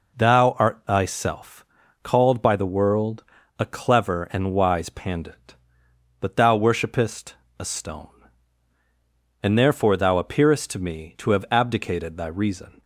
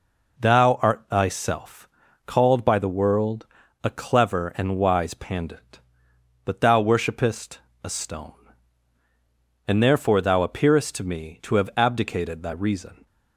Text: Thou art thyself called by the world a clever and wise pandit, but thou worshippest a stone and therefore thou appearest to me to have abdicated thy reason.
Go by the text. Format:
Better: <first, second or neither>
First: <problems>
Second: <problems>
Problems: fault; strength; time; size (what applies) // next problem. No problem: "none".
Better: neither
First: pauses between "thyself" and "called"; at 1.6 s; 0.38 s long // pauses between "world" and "a"; slight; at 3.2 s; 0.36 s long // pauses between "worshippest" and "a"; slight; at 7.3 s; 0.24 s long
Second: pauses between "thyself" and "called"; at 1.8 s; 0.38 s long // pauses between "world" and "a"; at 3.4 s; 0.38 s long // pauses between "worshippest" and "a"; slight; at 7.5 s; 0.24 s long